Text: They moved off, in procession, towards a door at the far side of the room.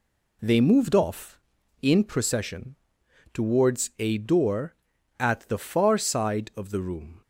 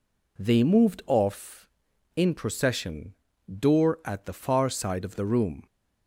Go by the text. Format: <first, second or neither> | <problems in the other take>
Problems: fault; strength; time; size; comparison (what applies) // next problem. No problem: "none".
first | skips "towards a"; at 3.3 s